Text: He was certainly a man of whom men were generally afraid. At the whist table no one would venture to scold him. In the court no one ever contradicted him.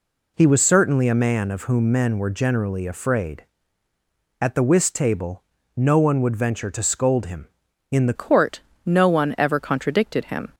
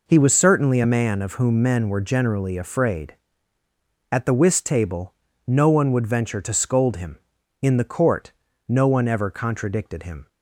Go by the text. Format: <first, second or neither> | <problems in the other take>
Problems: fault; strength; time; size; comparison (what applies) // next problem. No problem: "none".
second | pauses between "table" and "no"; slight; at 5.4 s; 0.34 s long; slight in the second // changes voice at "court"; from 8.1 s on; 2.4 s long // pauses between "court" and "no"; slight; at 8.6 s; 0.26 s long; slight in the second